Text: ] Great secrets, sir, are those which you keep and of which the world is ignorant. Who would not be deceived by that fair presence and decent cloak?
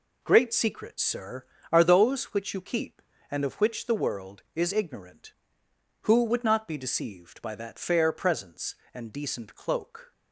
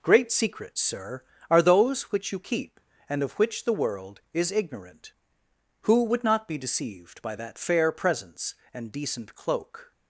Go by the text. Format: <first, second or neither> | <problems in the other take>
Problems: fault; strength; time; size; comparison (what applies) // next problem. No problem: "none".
neither | none